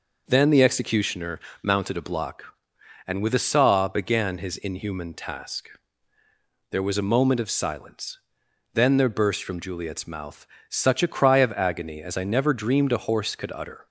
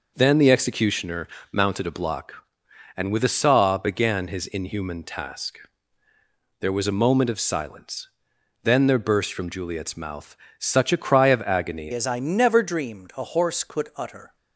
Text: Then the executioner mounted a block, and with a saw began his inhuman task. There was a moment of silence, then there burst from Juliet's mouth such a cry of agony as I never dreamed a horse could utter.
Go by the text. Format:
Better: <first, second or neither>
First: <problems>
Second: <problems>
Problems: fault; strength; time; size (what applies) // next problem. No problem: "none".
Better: first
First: pauses between "executioner" and "mounted"; slight; at 1.3 s; 0.23 s long // pauses between "mouth" and "such"; slight; at 10.4 s; 0.20 s long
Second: pauses between "executioner" and "mounted"; slight; at 1.2 s; 0.24 s long // pauses between "mouth" and "such"; slight; at 10.3 s; 0.20 s long // changes voice at "as"; from 11.9 s on; 2.4 s long